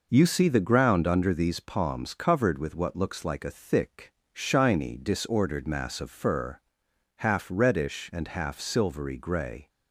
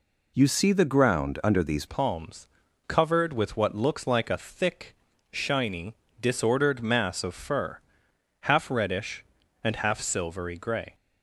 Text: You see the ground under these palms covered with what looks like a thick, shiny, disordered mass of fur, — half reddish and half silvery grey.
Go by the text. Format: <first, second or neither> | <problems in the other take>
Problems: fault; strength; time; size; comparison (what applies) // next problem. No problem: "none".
first | changes voice at "palms"; from 1.8 s on; 9.1 s long // pauses between "palms" and "covered"; at 2.4 s; 0.40 s long